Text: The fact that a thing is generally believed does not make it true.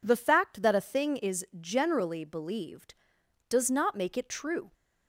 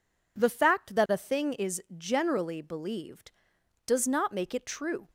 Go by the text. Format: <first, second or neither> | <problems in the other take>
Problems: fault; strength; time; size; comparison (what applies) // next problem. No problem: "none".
neither | pauses between "is" and "generally"; slight; the same in both